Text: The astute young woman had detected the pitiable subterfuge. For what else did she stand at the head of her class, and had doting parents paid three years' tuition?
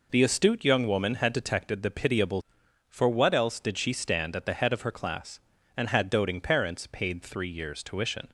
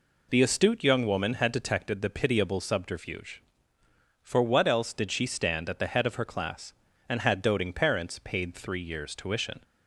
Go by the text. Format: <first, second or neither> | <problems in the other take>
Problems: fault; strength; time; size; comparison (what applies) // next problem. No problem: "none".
second | skips "subterfuge"; at 2.6 s